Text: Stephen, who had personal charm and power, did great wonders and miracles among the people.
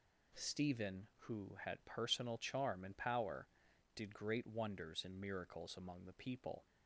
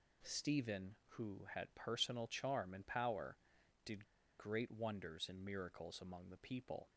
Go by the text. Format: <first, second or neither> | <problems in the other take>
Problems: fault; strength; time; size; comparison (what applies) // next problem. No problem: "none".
first | pauses between "did" and "great"; slight; at 4.0 s; 0.33 s long